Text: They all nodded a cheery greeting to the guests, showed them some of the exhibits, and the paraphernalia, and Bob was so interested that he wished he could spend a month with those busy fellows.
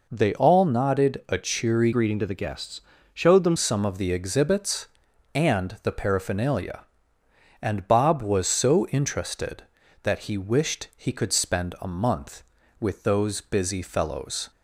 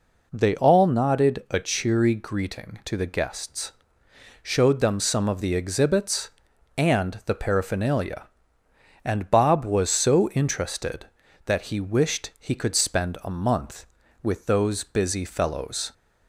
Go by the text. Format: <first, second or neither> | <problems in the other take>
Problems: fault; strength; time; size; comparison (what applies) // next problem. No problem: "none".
second | changes voice from "greeting" to "them"; from 1.9 to 3.5 s; 1.6 s long